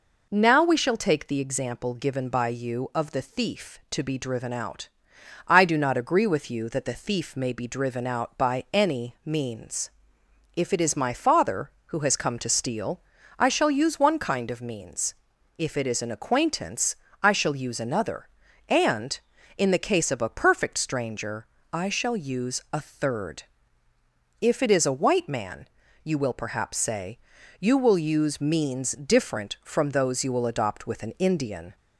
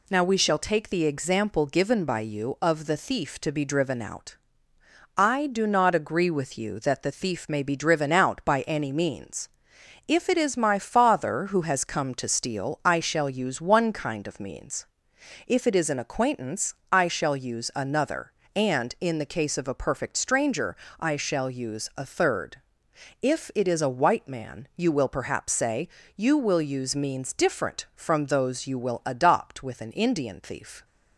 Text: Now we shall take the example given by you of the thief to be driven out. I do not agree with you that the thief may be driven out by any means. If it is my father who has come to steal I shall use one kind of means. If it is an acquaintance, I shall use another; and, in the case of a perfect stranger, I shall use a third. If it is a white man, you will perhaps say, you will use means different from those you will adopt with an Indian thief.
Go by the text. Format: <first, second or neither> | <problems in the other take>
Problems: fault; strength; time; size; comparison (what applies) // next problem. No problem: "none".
second | pauses between "steal" and "I"; at 13.0 s; 0.38 s long // stops before "thief"; at 31.7 s